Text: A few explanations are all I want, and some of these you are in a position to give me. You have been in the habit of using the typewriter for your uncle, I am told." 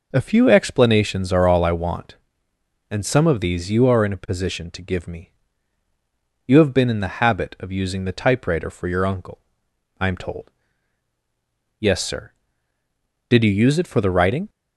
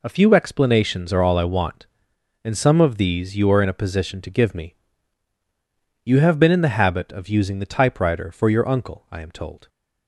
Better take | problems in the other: second | goes on to say "Yes sir Did you use it for the writing"; strong; from 11.7 s on; 2.7 s long

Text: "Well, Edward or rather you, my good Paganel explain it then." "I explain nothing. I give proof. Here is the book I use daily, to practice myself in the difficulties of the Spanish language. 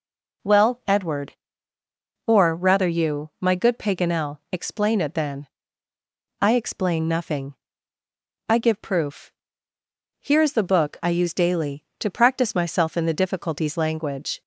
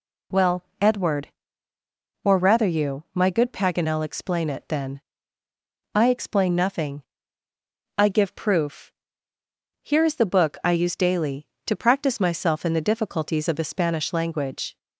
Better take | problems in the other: second | pauses between "Paganel" and "explain"; slight; at 4.3 s; 0.16 s long // skips "of the Spanish"; at 13.7 s

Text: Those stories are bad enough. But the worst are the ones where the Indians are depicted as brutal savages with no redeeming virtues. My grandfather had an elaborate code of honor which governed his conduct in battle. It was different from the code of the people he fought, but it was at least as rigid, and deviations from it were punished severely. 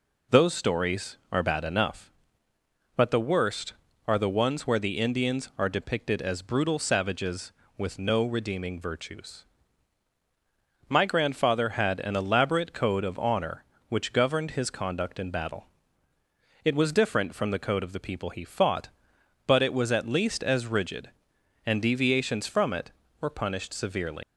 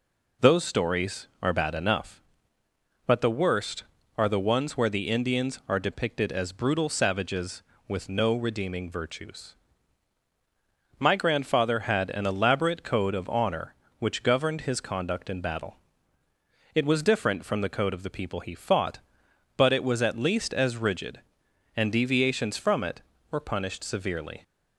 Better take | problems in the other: second | leaves "severely" unfinished; at 24.2 s; 95 ms

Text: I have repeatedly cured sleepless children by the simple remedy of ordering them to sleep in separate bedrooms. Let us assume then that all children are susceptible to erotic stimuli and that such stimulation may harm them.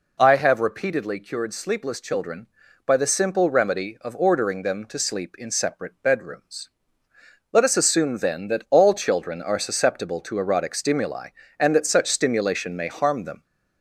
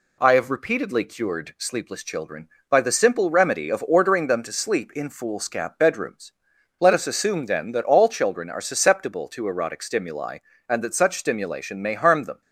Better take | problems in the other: first | says "foolscap" for "separate"; at 5.0 s

